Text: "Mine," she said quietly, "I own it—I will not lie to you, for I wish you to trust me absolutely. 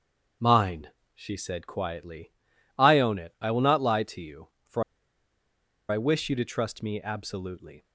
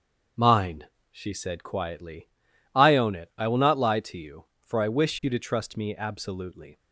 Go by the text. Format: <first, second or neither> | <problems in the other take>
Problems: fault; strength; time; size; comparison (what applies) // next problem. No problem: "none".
second | starts louder than the rest; strong; until 1.6 s; 7.5 dB; also in the second // pauses between "for" and "I"; at 4.8 s; 1.0 s long